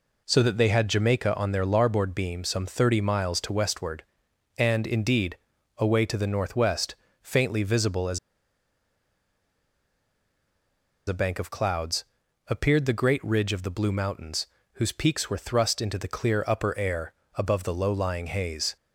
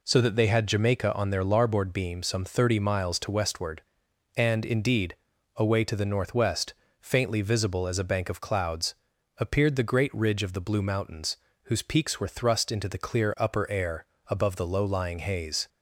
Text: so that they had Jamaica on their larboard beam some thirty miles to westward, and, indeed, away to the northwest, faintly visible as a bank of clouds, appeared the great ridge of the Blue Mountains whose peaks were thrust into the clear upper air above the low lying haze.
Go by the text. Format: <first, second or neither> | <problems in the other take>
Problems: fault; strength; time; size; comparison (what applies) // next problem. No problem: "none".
second | pauses between "as" and "a"; strong; at 8.1 s; 2.8 s long // pauses between "Mountains" and "whose"; slight; at 14.4 s; 0.28 s long; slight in the second // pauses between "air" and "above"; slight; at 17.1 s; 0.24 s long; slight in the second